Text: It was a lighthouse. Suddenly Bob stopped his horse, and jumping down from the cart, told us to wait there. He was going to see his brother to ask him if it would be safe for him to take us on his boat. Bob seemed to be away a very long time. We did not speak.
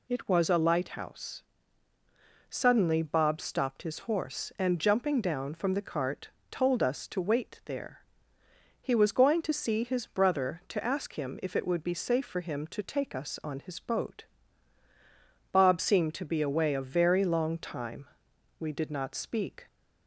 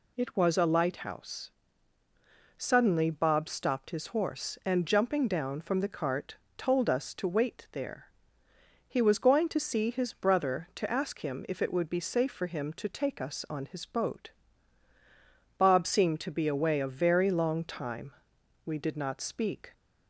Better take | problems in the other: neither | none

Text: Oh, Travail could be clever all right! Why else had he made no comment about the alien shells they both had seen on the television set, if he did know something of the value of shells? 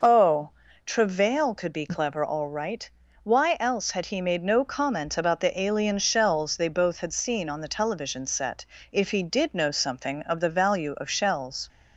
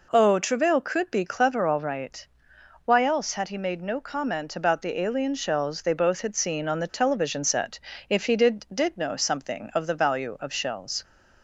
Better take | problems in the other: first | says "did" twice; at 8.7 s

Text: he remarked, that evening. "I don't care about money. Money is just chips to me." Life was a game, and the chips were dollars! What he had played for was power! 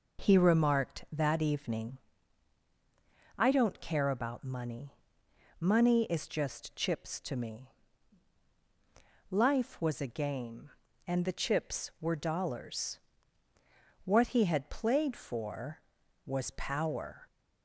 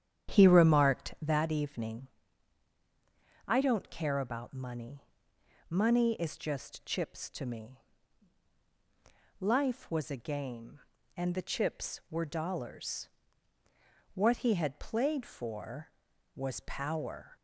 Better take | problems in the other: first | starts louder than the rest; strong; until 1.5 s; 9 dB

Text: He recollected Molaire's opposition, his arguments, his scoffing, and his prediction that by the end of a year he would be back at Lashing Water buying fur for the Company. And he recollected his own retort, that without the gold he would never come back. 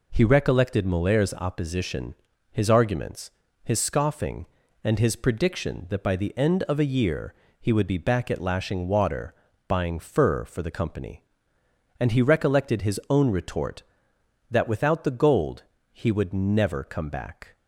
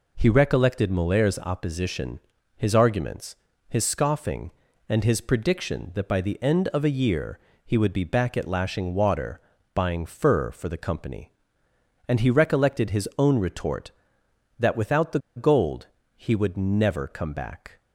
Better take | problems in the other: first | pauses between "year" and "he"; slight; at 7.3 s; 0.28 s long; slight in the first // pauses between "Water" and "buying"; slight; at 9.3 s; 0.34 s long; slight in the first // pauses between "the" and "gold"; slight; at 15.1 s; 0.18 s long // pauses between "gold" and "he"; slight; at 15.8 s; 0.28 s long; slight in the first

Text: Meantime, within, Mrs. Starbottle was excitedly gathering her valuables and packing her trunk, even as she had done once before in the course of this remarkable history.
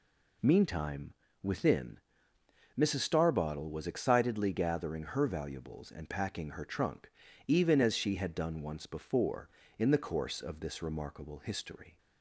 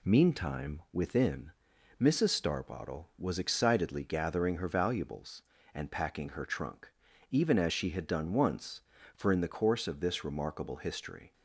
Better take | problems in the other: first | says "for" for "before"; at 9.1 s

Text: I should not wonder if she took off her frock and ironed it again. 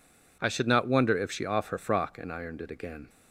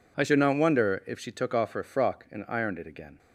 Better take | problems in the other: second | skips "took"; at 1.4 s

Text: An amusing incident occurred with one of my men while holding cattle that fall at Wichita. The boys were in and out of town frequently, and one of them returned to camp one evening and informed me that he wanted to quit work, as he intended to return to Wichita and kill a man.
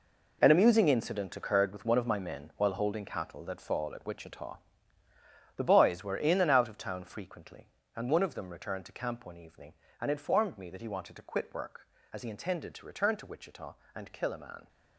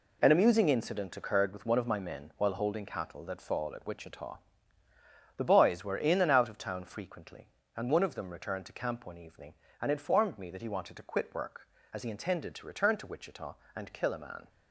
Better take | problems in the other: second | gets quieter; strong; throughout; 11.5 dB

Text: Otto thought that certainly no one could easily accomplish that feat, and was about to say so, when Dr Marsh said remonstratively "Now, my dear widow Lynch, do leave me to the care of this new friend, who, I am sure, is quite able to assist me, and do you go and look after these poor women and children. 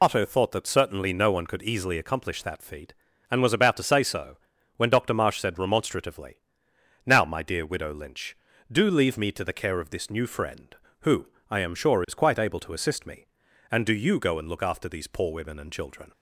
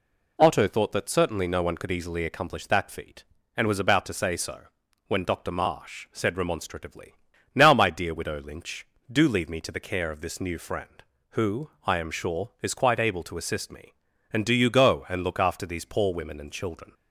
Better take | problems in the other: second | loses the start of "Otto"; at 0.0 s; 85 ms // pauses between "remonstratively" and "Now"; noticeable; at 6.3 s; 0.66 s long; also in the second

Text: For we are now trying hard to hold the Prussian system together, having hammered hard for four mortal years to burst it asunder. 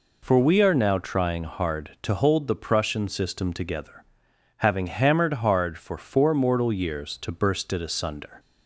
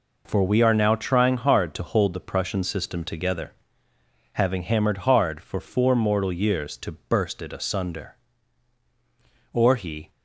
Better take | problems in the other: first | goes on to say "Or he"; from 9.5 s on; 0.58 s long

